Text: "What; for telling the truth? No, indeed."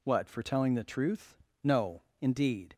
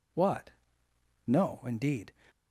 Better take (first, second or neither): first